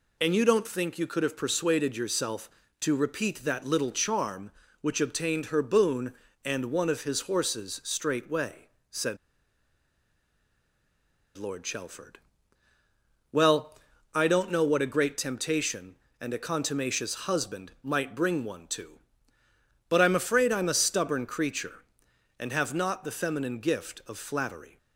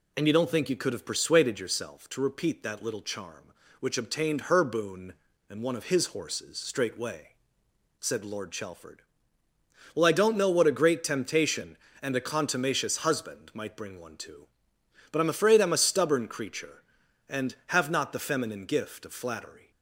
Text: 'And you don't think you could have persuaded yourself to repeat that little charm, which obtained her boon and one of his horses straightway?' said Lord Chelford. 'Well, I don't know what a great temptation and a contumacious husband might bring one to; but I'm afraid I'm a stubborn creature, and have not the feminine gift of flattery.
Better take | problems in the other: second | pauses between "said" and "Lord"; strong; at 9.1 s; 2.2 s long

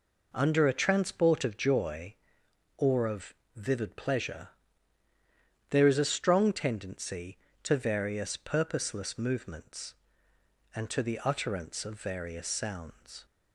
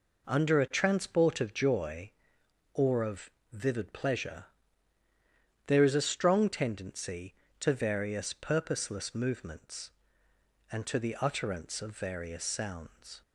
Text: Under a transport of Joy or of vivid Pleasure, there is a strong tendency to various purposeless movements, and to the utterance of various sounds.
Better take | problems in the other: neither | pauses between "of" and "vivid"; slight; the same in both

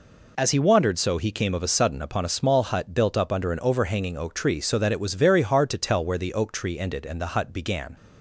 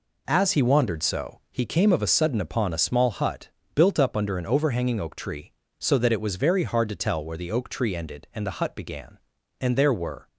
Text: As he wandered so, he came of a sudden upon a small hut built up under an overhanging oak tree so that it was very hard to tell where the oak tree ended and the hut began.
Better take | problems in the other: first | pauses between "hut" and "built"; slight; at 3.4 s; 0.26 s long // goes on to say "And there were"; noticeable; from 9.6 s on; 0.66 s long

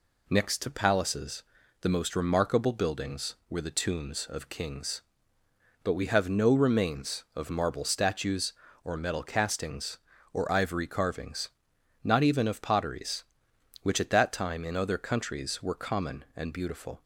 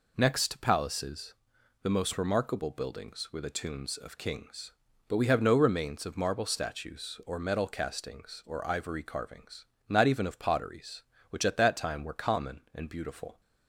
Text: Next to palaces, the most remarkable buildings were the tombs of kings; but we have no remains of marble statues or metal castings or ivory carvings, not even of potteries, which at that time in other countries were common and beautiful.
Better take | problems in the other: first | skips "in other countries"; at 12.0 s

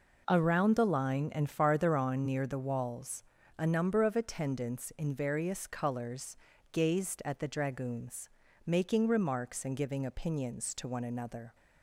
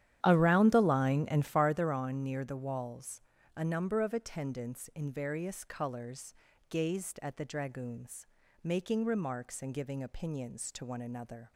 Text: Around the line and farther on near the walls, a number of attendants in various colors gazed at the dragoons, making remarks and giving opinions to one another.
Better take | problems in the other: first | starts louder than the rest; strong; until 1.8 s; 11 dB // pauses between "colors" and "gazed"; slight; at 6.3 s; 0.34 s long; slight in the first

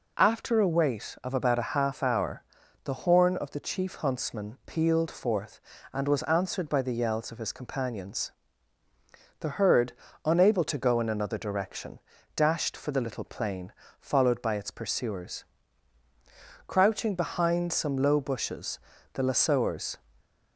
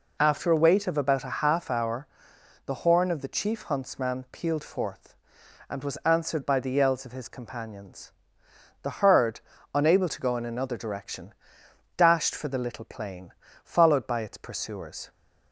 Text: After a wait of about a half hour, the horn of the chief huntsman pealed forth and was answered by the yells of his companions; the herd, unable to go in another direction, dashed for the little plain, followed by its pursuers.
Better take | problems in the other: second | goes on to say "Crouching behind some low bushes the lassoers"; strong; from 16.6 s on; 3.2 s long

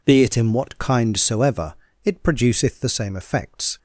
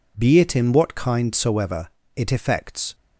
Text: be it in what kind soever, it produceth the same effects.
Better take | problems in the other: first | skips "produceth the same"; at 2.3 s

